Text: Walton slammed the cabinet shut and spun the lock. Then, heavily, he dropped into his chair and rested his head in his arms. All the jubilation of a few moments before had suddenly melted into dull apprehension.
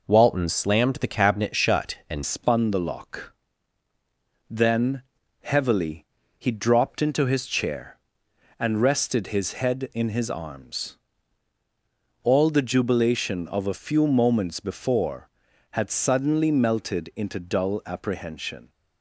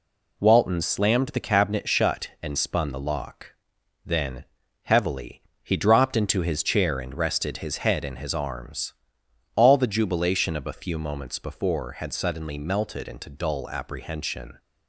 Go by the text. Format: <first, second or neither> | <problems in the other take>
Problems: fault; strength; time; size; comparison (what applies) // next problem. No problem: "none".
second | changes voice at "spun"; from 2.2 s on; 16.4 s long